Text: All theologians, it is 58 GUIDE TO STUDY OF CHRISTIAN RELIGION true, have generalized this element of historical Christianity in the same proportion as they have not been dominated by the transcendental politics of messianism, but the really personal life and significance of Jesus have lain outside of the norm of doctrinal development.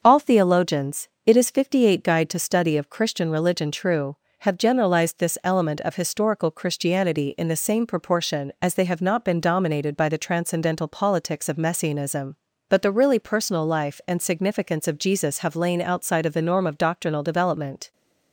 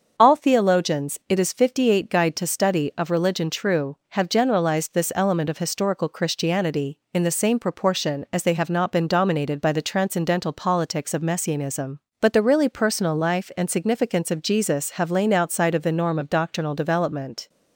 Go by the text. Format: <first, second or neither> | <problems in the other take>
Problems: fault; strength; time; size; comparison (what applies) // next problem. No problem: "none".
first | starts louder than the rest; until 1.1 s; 6.5 dB; also in the first // skips "CHRISTIAN"; at 3.0 s